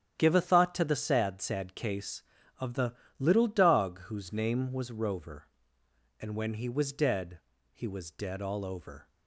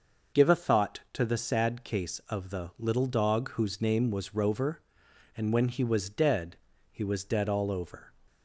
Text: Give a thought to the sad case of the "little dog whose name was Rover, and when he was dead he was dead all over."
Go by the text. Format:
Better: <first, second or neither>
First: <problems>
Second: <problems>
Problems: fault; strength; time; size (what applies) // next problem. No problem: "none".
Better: second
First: starts louder than the rest; strong; until 1.2 s; 10.5 dB // says "sad" twice; at 1.4 s // pauses between "the" and "little"; slight; at 2.9 s; 0.24 s long // pauses between "dead" and "he"; slight; at 7.3 s; 0.34 s long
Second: pauses between "dead" and "he"; slight; at 6.5 s; 0.36 s long